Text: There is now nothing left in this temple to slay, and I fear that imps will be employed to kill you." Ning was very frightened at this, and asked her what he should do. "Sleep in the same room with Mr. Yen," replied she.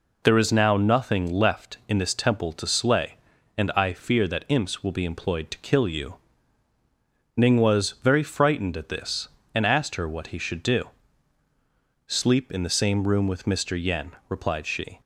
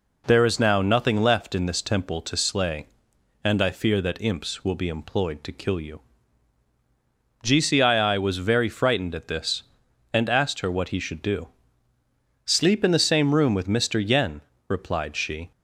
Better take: first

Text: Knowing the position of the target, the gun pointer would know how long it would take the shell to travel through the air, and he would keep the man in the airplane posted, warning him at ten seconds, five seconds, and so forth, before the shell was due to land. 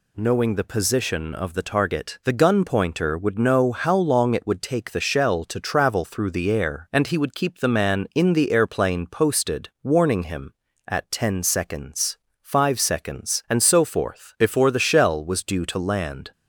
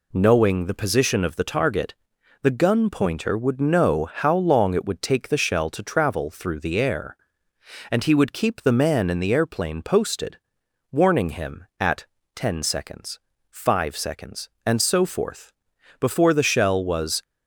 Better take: first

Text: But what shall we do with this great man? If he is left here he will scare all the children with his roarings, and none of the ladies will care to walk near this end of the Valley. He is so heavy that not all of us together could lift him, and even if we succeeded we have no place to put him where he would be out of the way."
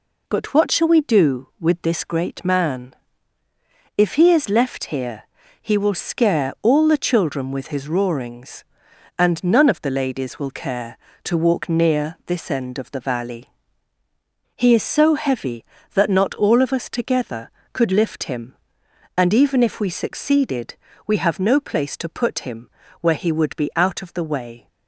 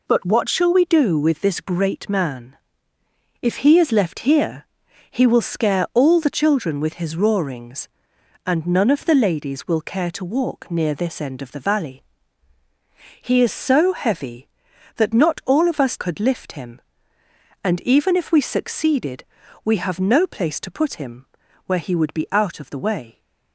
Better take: first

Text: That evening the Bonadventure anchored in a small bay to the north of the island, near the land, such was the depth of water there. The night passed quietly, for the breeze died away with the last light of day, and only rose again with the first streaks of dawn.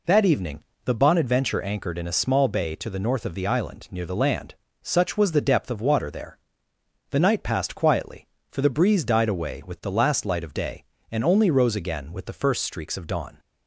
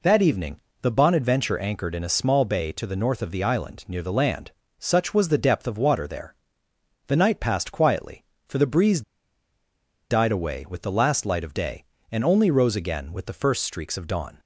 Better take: first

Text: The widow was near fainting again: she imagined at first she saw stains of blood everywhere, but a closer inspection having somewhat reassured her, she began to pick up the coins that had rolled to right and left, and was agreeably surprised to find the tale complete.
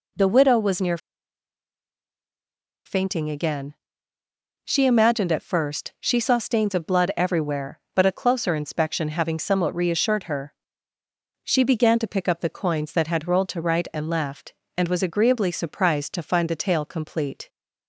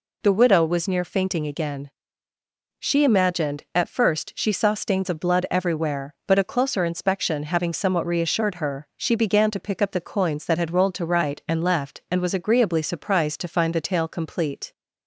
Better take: second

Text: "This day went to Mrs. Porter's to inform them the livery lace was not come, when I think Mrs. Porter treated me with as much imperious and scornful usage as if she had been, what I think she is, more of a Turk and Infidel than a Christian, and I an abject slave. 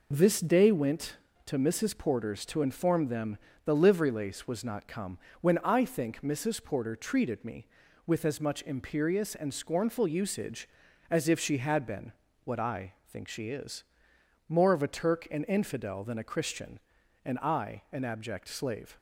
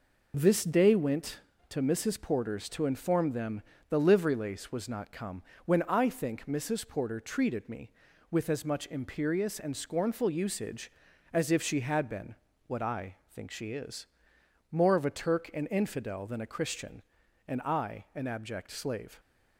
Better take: neither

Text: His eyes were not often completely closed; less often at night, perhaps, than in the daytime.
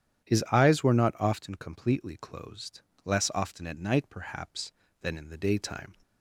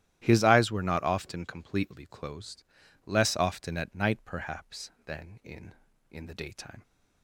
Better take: first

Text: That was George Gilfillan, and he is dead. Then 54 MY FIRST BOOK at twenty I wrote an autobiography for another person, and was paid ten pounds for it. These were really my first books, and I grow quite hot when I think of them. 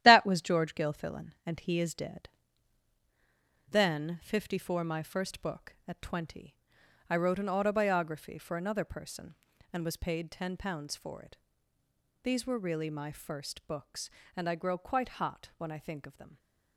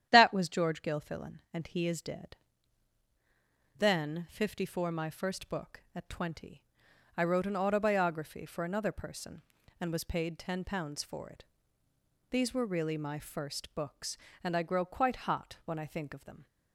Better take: second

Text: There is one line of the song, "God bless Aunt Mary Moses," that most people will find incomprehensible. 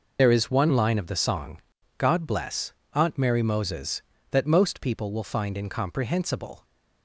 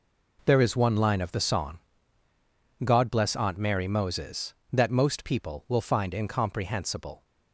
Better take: second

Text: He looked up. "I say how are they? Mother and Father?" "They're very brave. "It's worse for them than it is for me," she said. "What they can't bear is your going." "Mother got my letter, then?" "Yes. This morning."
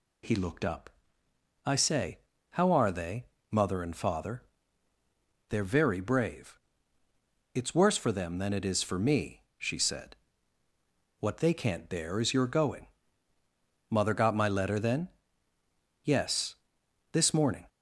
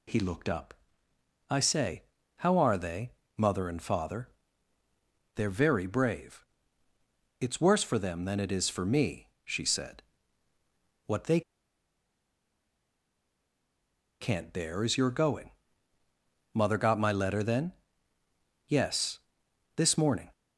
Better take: first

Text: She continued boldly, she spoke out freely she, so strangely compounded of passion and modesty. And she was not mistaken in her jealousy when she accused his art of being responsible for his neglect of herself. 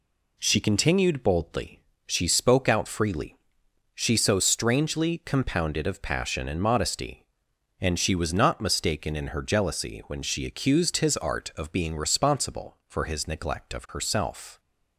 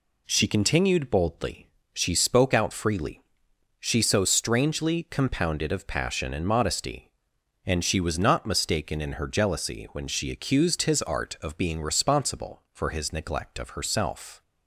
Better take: neither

